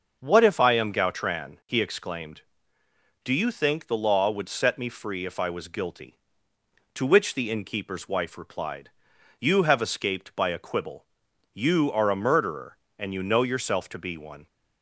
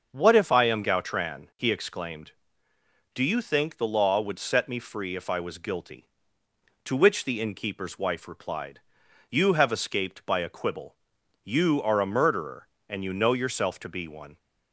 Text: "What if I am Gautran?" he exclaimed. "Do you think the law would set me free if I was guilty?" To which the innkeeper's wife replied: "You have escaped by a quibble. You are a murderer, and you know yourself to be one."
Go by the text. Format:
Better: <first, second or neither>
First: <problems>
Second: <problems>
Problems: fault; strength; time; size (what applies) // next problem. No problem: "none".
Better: neither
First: starts louder than the rest; noticeable; until 1.2 s; 6 dB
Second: starts louder than the rest; until 1.1 s; 6 dB